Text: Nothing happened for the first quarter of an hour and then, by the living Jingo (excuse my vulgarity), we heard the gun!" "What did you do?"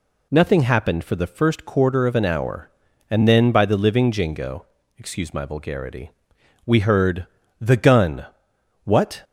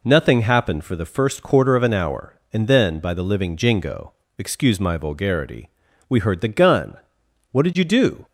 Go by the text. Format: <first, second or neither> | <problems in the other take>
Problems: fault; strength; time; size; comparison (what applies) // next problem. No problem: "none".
second | pauses between "heard" and "the"; slight; at 7.2 s; 0.35 s long // stops before "did you do"; at 9.2 s